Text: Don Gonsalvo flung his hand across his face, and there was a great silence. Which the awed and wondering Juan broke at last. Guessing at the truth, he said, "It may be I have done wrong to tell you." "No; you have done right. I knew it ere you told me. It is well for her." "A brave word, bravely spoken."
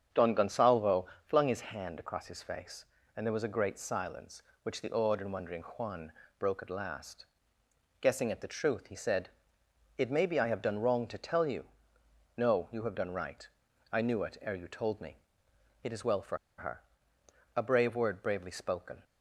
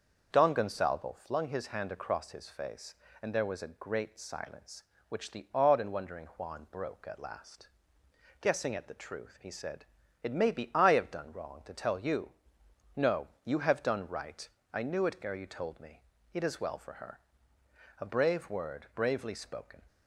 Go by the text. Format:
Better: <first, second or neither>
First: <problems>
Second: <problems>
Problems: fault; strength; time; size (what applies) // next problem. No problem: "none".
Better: second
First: starts louder than the rest; strong; until 1.3 s; 7.5 dB // pauses between "Gonsalvo" and "flung"; slight; at 1.0 s; 0.20 s long // pauses between "Juan" and "broke"; slight; at 6.1 s; 0.26 s long // pauses between "for" and "her"; slight; at 16.3 s; 0.21 s long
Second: starts louder than the rest; until 1.3 s; 6.5 dB